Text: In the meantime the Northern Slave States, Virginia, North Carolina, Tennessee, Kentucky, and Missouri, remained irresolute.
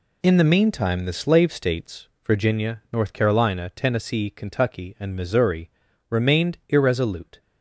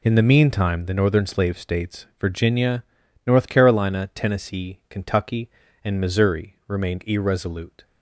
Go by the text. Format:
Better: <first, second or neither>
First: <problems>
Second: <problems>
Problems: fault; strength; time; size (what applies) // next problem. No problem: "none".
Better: second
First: skips "Northern"; at 1.1 s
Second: none